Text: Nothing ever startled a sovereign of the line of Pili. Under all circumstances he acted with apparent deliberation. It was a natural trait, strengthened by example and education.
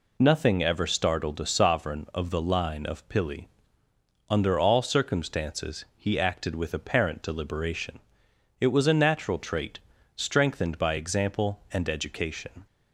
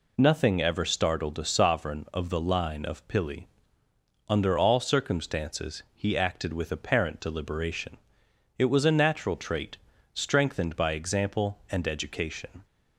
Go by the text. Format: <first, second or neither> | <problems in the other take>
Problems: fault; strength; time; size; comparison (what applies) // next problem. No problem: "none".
neither | none